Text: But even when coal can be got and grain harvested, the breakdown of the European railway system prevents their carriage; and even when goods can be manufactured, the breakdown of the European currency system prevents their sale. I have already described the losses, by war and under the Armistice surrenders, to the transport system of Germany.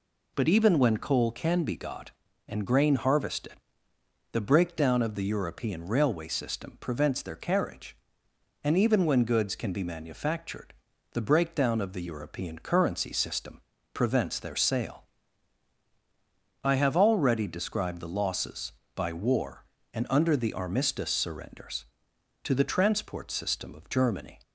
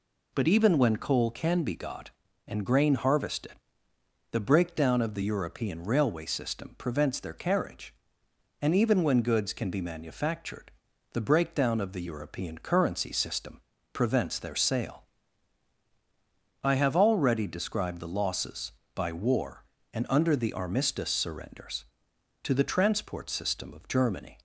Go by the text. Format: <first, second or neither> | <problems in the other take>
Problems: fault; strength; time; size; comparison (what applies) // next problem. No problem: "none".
neither | pauses between "system" and "prevents"; slight; the same in both